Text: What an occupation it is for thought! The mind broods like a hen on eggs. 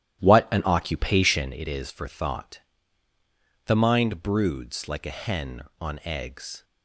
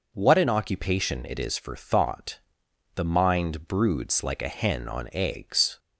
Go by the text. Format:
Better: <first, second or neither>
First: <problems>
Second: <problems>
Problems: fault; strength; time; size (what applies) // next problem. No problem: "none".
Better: second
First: starts louder than the rest; strong; until 1.6 s; 12 dB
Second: none